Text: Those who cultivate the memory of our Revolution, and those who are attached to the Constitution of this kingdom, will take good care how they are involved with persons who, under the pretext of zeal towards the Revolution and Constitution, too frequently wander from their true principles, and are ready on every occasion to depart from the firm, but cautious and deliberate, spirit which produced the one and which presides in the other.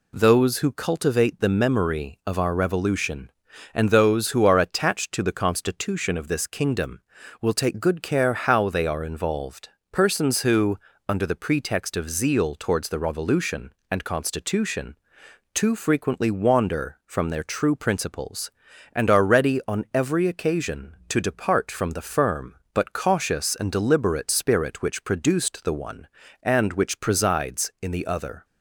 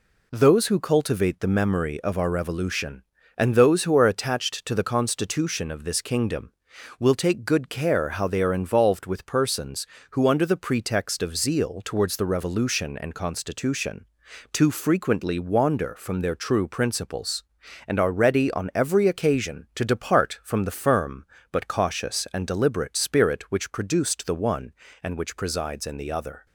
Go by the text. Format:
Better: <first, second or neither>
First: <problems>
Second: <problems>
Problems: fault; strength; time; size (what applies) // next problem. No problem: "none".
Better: second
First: skips "with"; at 9.8 s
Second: none